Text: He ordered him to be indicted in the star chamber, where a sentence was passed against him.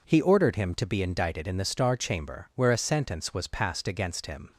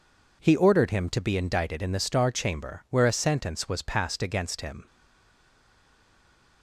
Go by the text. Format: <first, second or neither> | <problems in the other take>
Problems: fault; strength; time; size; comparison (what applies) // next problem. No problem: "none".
first | stays silent after the last word; noticeable; from 4.8 s on; 1.8 s long